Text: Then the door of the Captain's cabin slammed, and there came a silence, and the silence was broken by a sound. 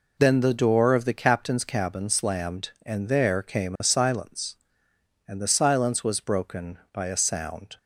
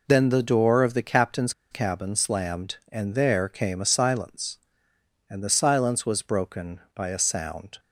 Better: first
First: none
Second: pauses between "Captain's" and "cabin"; slight; at 1.5 s; 0.19 s long

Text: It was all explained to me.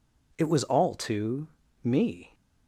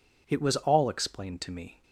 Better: second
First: skips "explained"; at 0.9 s // pauses between "to" and "me"; at 1.4 s; 0.38 s long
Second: none

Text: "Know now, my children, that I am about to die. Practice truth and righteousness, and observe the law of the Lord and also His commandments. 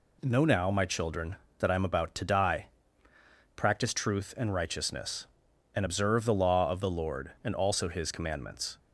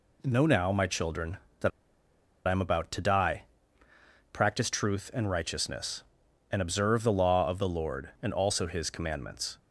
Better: first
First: none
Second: pauses between "that" and "I"; noticeable; at 1.7 s; 0.77 s long

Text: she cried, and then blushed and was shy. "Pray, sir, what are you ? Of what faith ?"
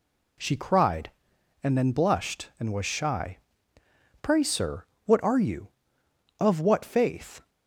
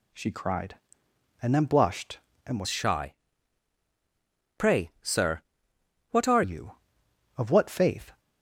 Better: first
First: none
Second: changes voice from "shy" to "are"; from 2.6 to 6.4 s; 3.8 s long

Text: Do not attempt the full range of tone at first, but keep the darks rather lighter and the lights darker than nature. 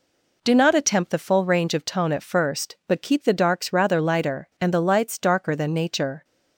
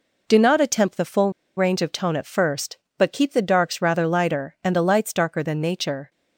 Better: first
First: none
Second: pauses between "full" and "range"; slight; at 1.2 s; 0.27 s long

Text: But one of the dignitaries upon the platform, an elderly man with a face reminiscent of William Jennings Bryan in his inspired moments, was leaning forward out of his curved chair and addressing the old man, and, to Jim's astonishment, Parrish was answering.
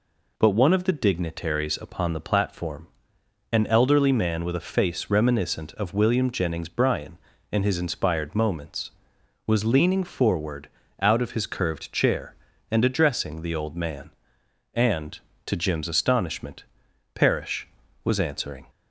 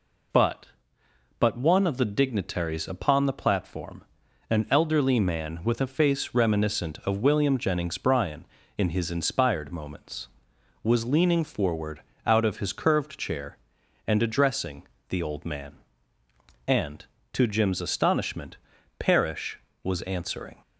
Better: first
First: pauses between "forward" and "out"; slight; at 10.6 s; 0.32 s long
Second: says "But" twice; at 1.3 s // pauses between "forward" and "out"; slight; at 12.0 s; 0.24 s long // pauses between "addressing" and "the"; slight; at 14.8 s; 0.26 s long

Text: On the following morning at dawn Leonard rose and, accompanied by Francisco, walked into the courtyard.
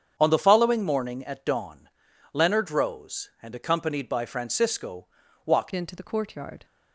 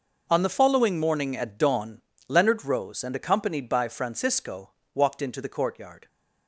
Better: second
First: starts louder than the rest; strong; until 1.1 s; 8 dB // pauses between "dawn" and "Leonard"; at 1.8 s; 0.44 s long // changes voice at "into"; from 5.7 s on; 0.9 s long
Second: pauses between "dawn" and "Leonard"; slight; at 2.0 s; 0.26 s long

